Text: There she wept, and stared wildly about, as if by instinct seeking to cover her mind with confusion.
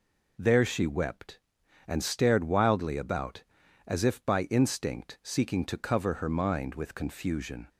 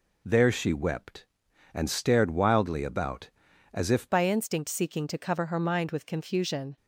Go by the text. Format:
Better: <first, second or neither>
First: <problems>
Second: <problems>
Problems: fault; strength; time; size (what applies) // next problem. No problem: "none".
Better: first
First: none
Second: changes voice at "by"; from 4.0 s on; 2.7 s long